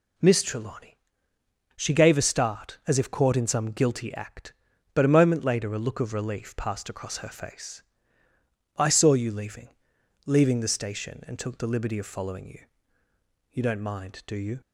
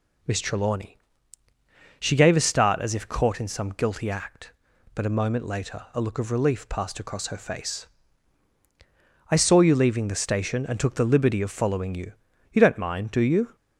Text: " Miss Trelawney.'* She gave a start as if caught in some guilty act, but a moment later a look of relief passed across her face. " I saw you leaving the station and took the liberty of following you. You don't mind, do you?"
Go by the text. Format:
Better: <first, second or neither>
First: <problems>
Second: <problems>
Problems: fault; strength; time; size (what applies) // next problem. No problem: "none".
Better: second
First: says "leaving" twice; at 10.2 s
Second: none